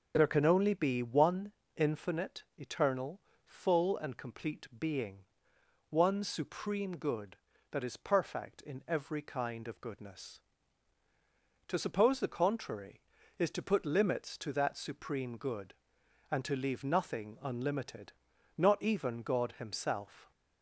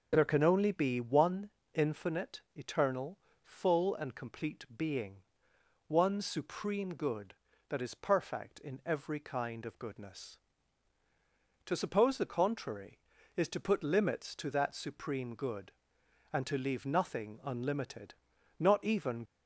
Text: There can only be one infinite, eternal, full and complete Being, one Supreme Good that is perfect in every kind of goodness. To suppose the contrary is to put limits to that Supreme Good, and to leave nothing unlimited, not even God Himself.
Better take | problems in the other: first | pauses between "one" and "infinite"; slight; at 1.4 s; 0.24 s long; slight in the first // stops before "God Himself"; at 19.2 s

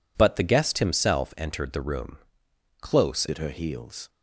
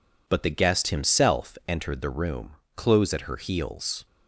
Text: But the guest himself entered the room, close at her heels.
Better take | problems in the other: second | changes voice at "at"; from 3.2 s on; 0.8 s long

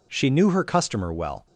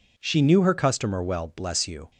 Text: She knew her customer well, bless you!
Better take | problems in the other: second | stops before "bless you"; at 1.4 s

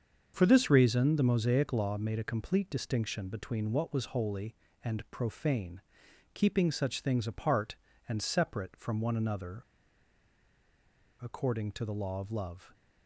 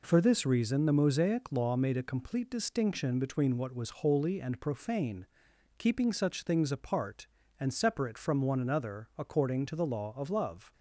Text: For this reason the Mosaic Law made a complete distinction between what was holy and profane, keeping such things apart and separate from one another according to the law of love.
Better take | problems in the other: second | starts louder than the rest; until 1.3 s; 6.5 dB // pauses between "another" and "according"; strong; at 9.6 s; 1.5 s long

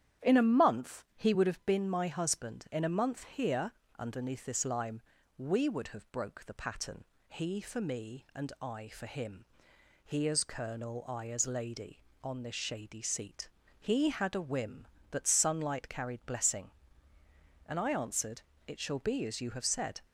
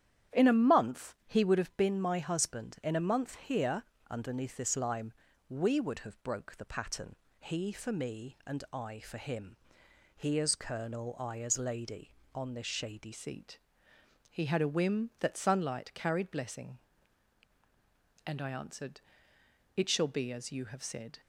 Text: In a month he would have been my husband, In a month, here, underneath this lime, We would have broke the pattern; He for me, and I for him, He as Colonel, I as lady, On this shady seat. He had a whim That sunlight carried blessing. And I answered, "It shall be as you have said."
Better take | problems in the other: first | starts louder than the rest; strong; until 1.4 s; 10 dB; strong in the first // changes voice at "seat"; from 13.1 s on; 8.1 s long

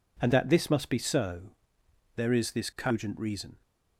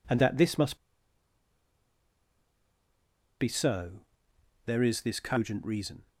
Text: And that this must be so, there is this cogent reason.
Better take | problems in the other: first | pauses between "must" and "be"; strong; at 0.7 s; 2.6 s long

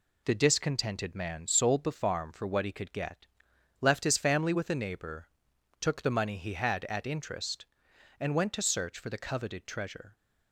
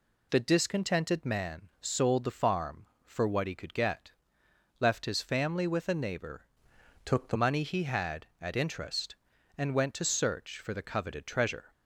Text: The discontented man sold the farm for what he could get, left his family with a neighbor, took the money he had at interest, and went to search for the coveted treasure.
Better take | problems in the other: first | changes voice from "took" to "the"; from 7.0 to 7.3 s; 0.3 s long

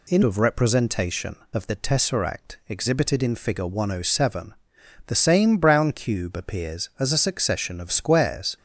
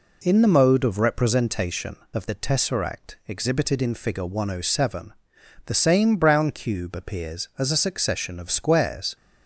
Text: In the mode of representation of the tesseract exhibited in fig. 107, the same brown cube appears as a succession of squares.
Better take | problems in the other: second | skips "the mode"; at 0.2 s

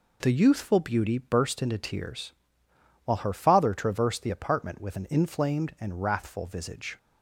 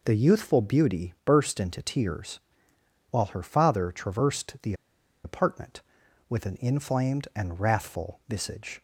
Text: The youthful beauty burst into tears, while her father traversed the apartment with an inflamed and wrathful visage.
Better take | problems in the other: first | pauses between "the" and "apartment"; noticeable; at 4.7 s; 0.51 s long

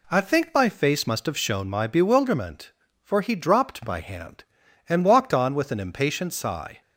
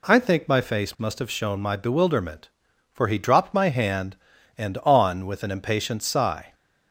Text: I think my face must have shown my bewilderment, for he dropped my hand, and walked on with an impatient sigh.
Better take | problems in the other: first | skips "walked"; at 4.8 s

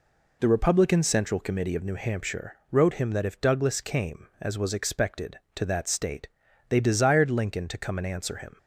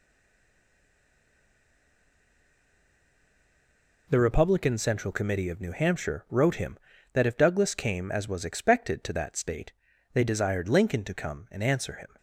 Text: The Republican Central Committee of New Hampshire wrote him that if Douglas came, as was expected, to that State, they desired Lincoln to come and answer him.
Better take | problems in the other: first | stays silent before the first word; strong; until 4.0 s; 4.0 s long

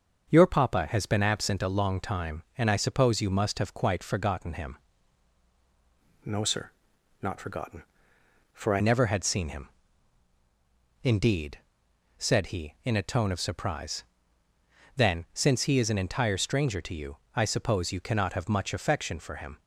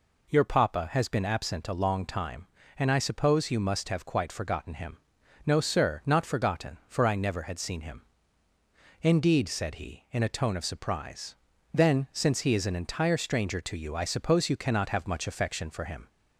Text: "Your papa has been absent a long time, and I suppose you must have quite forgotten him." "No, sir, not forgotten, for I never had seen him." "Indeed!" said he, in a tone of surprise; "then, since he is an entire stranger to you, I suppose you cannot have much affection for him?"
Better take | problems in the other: second | starts louder than the rest; until 1.3 s; 6.5 dB // changes voice from "No" to "I"; from 6.2 to 8.8 s; 2.6 s long

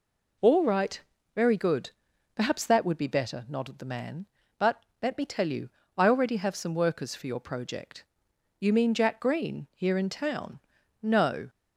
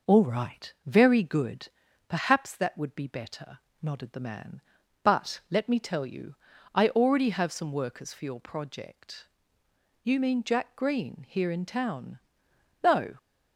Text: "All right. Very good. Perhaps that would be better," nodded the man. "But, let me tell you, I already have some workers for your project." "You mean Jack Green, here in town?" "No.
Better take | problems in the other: neither | none

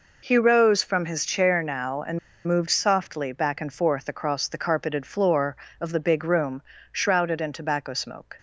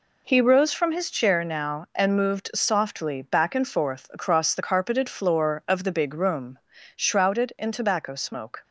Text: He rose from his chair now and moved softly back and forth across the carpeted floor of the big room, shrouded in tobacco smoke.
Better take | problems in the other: second | pauses between "and" and "moved"; slight; at 2.1 s; 0.28 s long

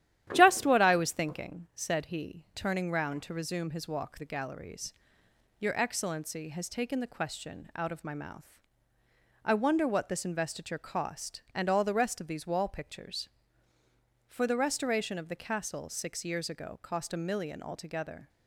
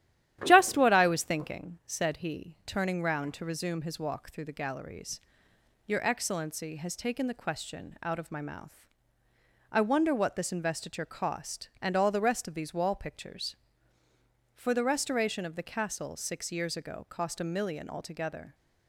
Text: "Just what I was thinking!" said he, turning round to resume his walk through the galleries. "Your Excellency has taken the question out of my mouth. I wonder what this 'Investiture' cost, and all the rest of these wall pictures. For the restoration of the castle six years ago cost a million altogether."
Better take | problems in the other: second | starts louder than the rest; strong; until 1.3 s; 11.5 dB; strong in the second // skips "through"; at 4.1 s

